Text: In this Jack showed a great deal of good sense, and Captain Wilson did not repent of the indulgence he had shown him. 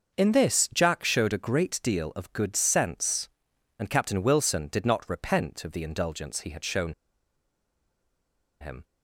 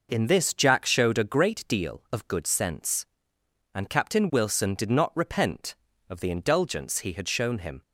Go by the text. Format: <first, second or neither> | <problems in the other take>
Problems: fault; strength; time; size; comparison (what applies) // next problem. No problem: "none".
second | starts louder than the rest; until 1.2 s; 6 dB // pauses between "shown" and "him"; strong; at 6.9 s; 1.6 s long